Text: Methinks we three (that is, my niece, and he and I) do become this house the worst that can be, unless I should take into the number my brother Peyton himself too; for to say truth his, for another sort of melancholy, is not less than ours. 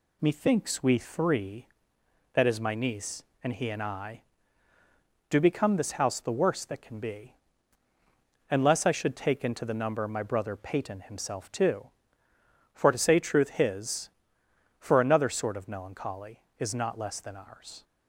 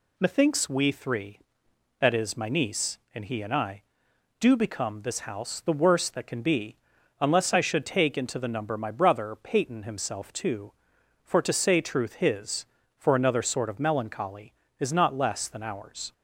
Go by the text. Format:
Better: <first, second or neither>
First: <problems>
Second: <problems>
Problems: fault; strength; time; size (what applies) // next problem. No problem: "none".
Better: neither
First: none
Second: none